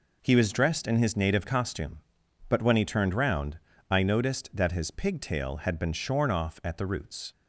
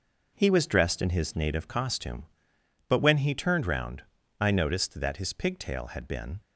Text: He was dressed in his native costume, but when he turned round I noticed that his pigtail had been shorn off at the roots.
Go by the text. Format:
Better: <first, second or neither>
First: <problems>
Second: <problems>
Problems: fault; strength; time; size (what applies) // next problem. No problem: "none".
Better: first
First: pauses between "round" and "I"; slight; at 3.5 s; 0.32 s long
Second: pauses between "round" and "I"; at 4.0 s; 0.38 s long // stops before "shorn off at the roots"; at 6.4 s